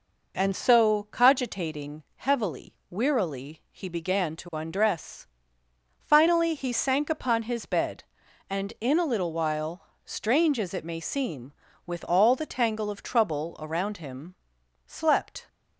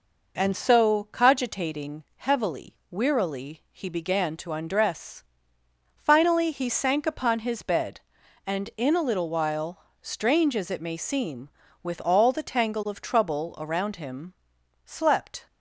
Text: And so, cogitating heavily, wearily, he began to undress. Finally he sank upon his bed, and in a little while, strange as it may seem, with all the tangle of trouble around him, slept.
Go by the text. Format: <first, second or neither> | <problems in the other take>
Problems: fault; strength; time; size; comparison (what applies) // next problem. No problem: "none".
neither | none